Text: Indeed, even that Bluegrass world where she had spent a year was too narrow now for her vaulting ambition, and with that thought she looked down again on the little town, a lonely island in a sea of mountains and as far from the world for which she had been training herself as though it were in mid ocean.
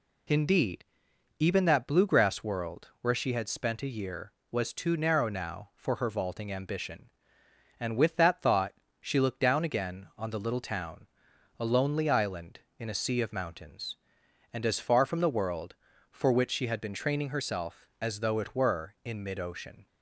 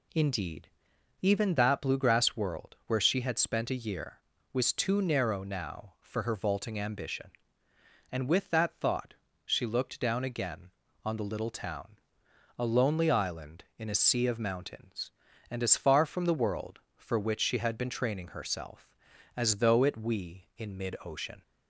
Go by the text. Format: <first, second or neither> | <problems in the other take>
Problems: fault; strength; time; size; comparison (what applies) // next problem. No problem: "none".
first | pauses between "thought" and "she"; slight; at 9.1 s; 0.28 s long; slight in the first // says "we" for "were"; at 19.9 s